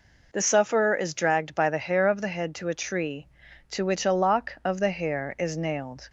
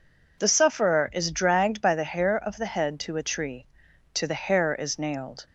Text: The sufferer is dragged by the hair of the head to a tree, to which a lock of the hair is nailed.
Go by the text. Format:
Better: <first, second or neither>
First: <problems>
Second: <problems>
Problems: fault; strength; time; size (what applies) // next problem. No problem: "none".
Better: first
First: none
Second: skips "which a lock of"; at 4.2 s